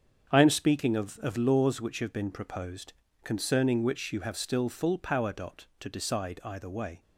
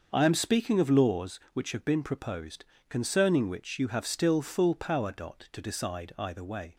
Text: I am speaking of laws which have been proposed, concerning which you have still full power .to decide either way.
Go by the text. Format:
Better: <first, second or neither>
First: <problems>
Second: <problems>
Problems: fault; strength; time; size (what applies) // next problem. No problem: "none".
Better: second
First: starts louder than the rest; strong; until 1.3 s; 7.5 dB // says "of" twice; at 1.1 s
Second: starts louder than the rest; until 1.1 s; 6.5 dB